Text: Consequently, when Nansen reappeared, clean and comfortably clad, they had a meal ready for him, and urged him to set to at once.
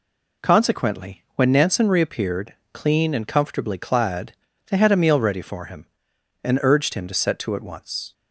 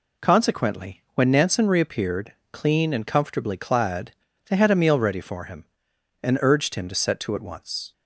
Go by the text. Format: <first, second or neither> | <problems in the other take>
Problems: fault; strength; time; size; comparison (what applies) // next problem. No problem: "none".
neither | none